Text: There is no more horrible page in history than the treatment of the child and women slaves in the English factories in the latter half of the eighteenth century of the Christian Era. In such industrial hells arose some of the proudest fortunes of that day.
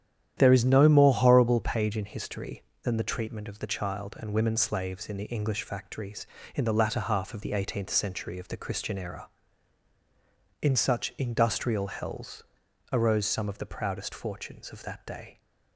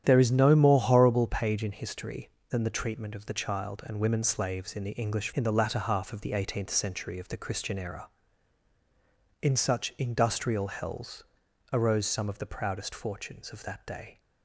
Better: first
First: starts louder than the rest; strong; until 1.3 s; 10 dB // pauses between "hells" and "arose"; noticeable; at 12.4 s; 0.50 s long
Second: starts louder than the rest; strong; until 1.0 s; 10 dB // skips "factories"; at 5.3 s // pauses between "hells" and "arose"; noticeable; at 11.2 s; 0.50 s long

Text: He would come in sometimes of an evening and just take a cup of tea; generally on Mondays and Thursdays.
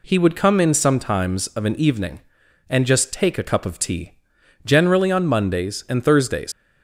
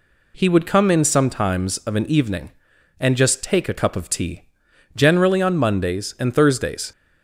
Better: second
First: leaves "Thursdays" unfinished; at 6.5 s; 90 ms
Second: none

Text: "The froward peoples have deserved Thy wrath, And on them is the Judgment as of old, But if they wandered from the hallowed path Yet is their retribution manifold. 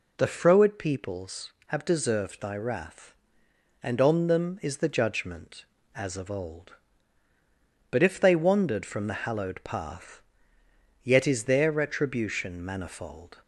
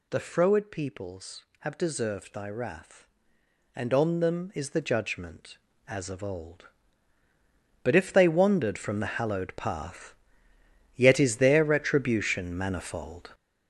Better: first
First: pauses between "path" and "Yet"; noticeable; at 10.2 s; 0.82 s long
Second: gets louder; strong; throughout; 7.5 dB // pauses between "path" and "Yet"; noticeable; at 10.1 s; 0.82 s long

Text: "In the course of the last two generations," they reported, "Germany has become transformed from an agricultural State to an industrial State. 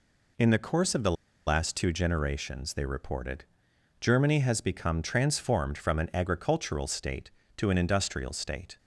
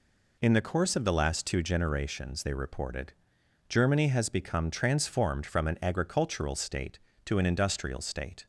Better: second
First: pauses between "the" and "last"; slight; at 1.1 s; 0.34 s long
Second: none

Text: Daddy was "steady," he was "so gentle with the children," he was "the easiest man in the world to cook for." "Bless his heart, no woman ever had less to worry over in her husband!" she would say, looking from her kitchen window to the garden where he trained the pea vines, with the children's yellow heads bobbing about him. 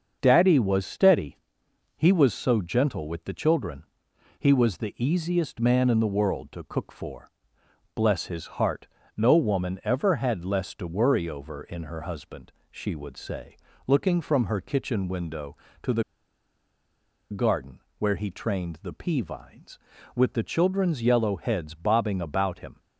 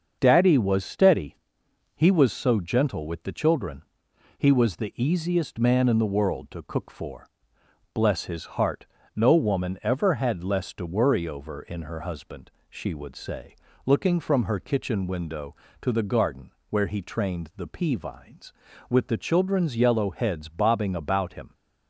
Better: second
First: starts louder than the rest; until 1.2 s; 6.5 dB // pauses between "the" and "garden"; strong; at 16.0 s; 1.2 s long // pauses between "garden" and "where"; slight; at 17.7 s; 0.18 s long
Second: starts louder than the rest; until 1.2 s; 6.5 dB // pauses between "garden" and "where"; slight; at 16.5 s; 0.18 s long

